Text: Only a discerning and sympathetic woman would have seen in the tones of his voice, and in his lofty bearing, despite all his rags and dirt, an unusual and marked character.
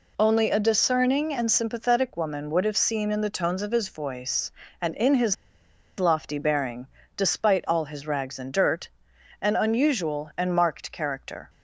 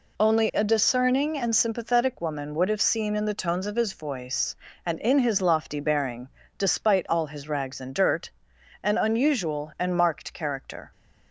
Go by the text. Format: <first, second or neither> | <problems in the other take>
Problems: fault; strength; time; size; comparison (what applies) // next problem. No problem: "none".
second | pauses between "his" and "lofty"; noticeable; at 5.3 s; 0.64 s long